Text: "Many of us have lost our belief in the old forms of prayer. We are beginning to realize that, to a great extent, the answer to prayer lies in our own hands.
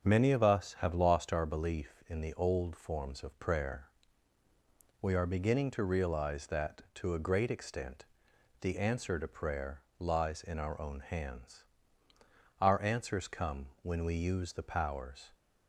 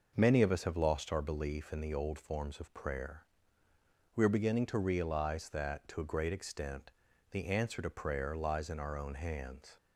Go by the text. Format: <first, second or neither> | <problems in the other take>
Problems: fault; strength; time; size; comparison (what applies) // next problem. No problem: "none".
second | starts louder than the rest; strong; until 1.1 s; 7 dB // pauses between "prayer" and "lies"; slight; at 9.8 s; 0.18 s long // goes on to say "Our answers come when we use the powers"; strong; from 12.5 s on; 2.7 s long